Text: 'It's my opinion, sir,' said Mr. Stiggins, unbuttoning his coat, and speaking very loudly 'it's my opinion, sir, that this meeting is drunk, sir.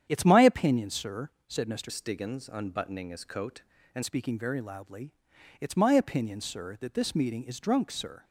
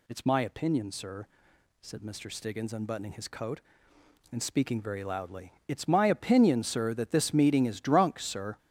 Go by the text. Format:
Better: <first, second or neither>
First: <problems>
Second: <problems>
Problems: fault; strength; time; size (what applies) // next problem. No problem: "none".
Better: second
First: starts louder than the rest; strong; until 1.1 s; 9 dB // changes voice from "Stiggins" to "and"; from 1.8 to 4.0 s; 2.2 s long // pauses between "loudly" and "it's"; noticeable; at 5.1 s; 0.48 s long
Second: none